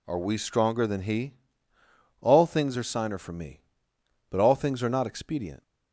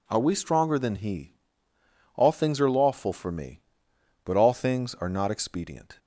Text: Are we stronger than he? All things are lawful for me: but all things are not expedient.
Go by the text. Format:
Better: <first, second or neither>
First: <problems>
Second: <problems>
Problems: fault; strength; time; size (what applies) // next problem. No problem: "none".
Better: second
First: says "signer" for "lawful"; at 2.8 s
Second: none